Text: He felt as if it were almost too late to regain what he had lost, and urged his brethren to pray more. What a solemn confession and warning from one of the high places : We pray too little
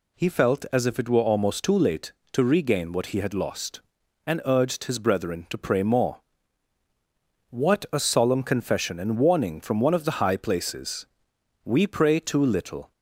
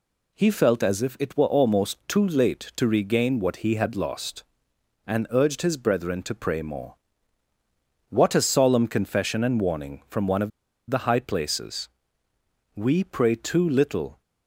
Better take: first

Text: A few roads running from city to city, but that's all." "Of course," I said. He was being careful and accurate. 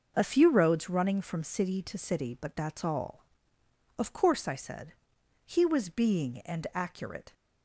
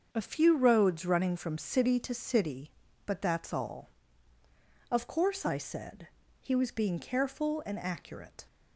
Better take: second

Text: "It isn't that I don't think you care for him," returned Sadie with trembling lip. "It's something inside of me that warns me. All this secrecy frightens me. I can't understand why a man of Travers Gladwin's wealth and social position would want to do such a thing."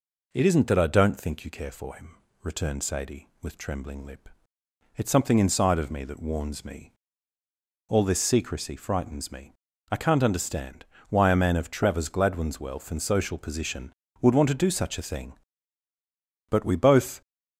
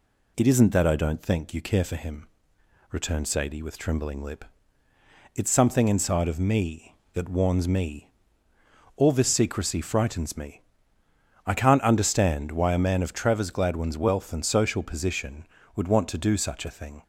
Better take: second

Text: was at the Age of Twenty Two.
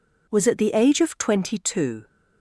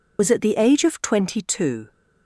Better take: first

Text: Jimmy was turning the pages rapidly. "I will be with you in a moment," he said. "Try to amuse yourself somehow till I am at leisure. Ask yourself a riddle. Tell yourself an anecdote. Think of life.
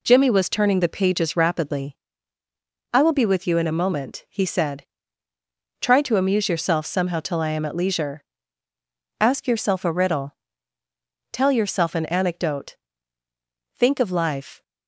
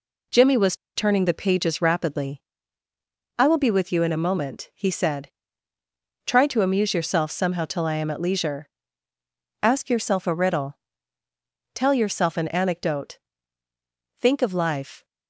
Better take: first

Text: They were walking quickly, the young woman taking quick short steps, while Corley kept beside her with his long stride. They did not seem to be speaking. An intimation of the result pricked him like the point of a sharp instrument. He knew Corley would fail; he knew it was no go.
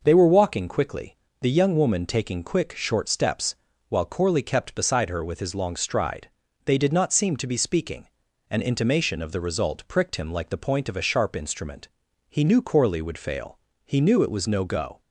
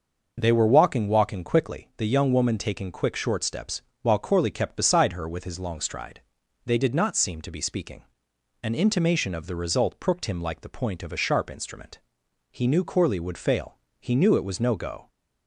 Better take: first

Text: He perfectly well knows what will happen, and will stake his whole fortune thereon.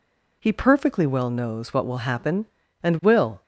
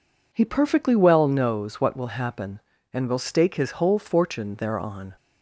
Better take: second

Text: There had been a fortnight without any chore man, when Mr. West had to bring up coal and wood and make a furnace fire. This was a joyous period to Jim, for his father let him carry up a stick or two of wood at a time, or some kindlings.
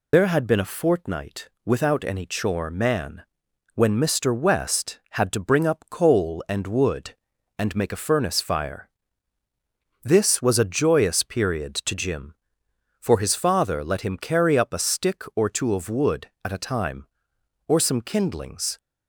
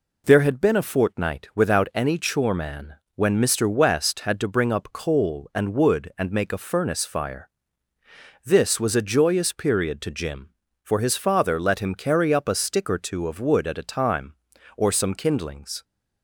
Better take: second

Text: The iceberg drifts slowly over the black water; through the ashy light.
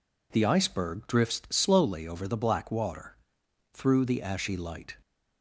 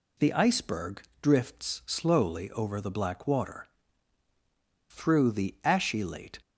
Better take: first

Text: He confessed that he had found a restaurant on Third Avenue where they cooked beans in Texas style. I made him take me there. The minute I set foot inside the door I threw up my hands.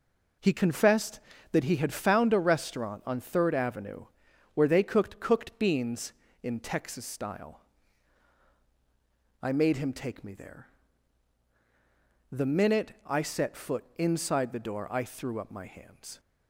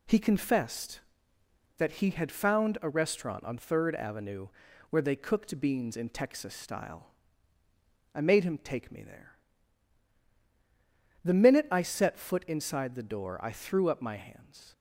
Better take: second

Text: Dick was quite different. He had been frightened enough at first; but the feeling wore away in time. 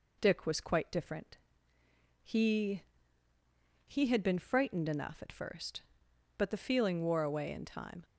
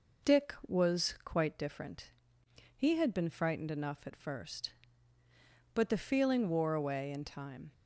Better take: second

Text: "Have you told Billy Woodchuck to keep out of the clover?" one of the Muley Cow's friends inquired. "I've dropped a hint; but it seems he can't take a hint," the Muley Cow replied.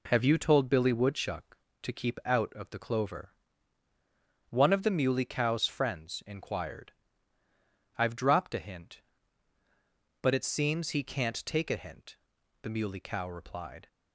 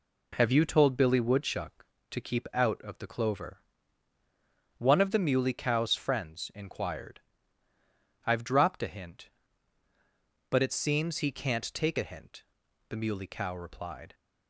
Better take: neither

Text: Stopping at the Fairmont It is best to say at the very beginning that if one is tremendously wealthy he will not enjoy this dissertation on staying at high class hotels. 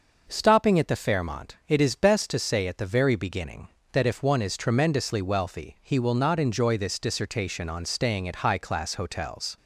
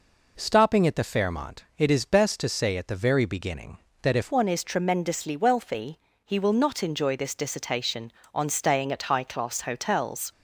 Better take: first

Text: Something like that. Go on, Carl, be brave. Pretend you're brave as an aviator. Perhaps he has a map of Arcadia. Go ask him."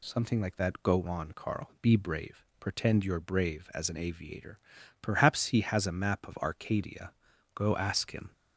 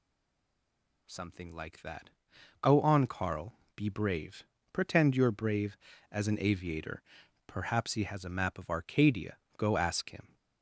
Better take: first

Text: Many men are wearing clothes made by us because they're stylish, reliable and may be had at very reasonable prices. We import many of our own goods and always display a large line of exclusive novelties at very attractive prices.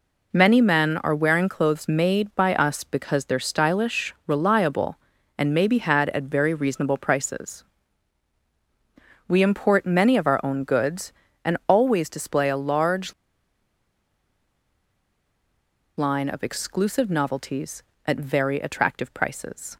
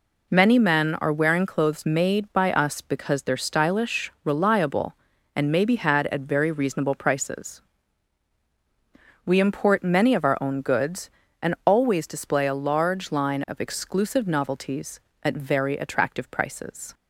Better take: second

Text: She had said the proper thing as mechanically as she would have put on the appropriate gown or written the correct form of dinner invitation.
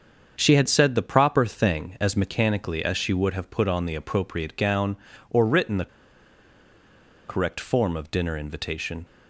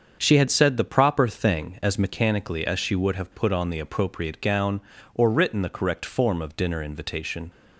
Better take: second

